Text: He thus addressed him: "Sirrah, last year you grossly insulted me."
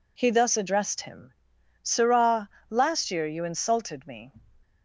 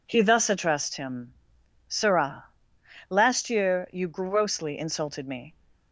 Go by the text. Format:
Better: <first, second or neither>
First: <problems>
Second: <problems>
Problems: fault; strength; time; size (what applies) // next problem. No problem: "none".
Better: second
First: skips "grossly"; at 3.4 s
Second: none